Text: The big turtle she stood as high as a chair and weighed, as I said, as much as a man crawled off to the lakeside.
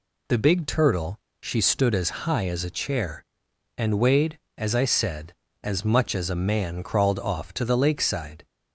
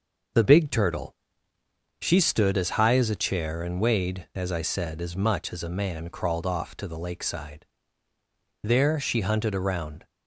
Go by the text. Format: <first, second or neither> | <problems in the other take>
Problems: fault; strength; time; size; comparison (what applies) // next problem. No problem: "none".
first | pauses between "turtle" and "she"; noticeable; at 1.1 s; 0.88 s long; slight in the first // goes on to say "There she hunted around"; from 8.6 s on; 1.4 s long